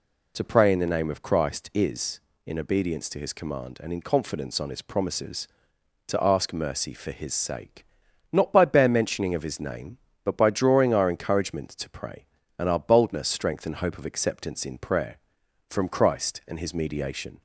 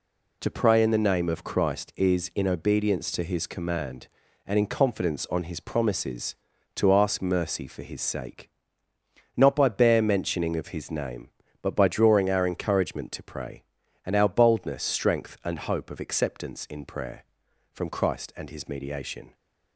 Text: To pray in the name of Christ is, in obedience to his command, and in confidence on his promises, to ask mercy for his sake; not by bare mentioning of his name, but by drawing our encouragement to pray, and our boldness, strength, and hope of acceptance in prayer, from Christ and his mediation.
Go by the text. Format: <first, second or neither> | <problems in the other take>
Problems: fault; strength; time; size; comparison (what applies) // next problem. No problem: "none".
neither | none